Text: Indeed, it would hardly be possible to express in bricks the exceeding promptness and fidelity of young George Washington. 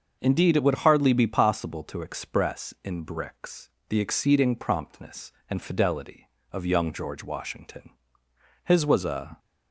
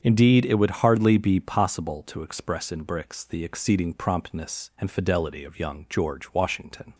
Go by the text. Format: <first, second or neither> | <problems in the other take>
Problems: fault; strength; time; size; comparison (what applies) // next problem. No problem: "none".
second | starts louder than the rest; until 1.2 s; 6.5 dB; strong in the second // pauses between "bricks" and "the"; slight; at 3.6 s; 0.20 s long // goes on to say "His was a"; noticeable; from 8.6 s on; 0.74 s long